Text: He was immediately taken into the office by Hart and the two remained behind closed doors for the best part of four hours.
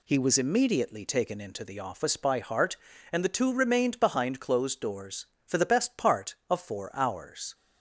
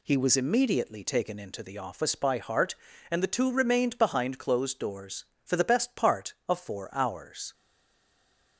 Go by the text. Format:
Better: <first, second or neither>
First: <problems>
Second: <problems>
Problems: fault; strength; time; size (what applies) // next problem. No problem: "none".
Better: first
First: none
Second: stays silent after the last word; from 7.5 s on; 1.0 s long